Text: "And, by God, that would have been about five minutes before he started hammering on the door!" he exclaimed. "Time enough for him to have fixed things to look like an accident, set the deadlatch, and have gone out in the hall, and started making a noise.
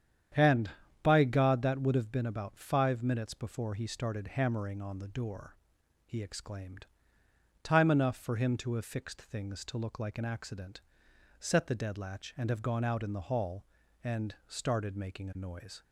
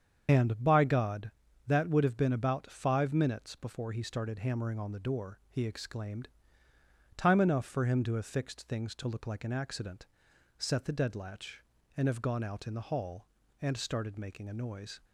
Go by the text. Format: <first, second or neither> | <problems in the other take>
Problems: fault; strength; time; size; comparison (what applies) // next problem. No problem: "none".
first | loses the start of "And"; at 0.2 s; 55 ms // starts louder than the rest; strong; until 1.2 s; 7.5 dB; strong in the first